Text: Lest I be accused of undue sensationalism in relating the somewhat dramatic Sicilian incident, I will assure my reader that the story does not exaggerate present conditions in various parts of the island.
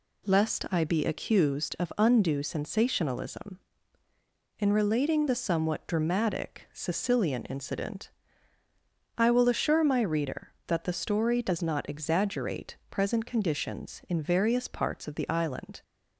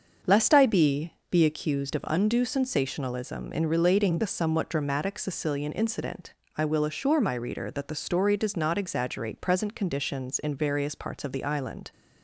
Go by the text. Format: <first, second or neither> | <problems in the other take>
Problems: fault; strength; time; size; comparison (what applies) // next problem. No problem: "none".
first | starts louder than the rest; until 1.4 s; 6.5 dB // says "be" twice; at 1.3 s